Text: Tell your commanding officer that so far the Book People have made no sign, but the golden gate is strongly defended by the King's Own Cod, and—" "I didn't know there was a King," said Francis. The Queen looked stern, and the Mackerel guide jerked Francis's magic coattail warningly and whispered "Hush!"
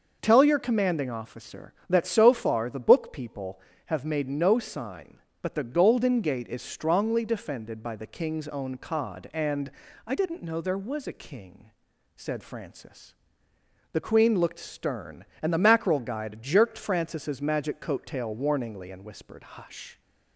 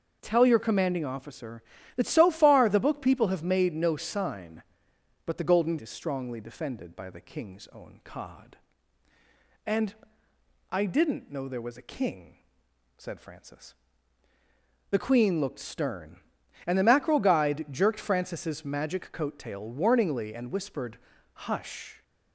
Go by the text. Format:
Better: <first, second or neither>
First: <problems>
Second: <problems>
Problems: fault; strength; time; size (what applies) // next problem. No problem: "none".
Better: first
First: none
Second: skips "gate"; at 5.7 s // pauses between "whispered" and "Hush"; slight; at 20.9 s; 0.34 s long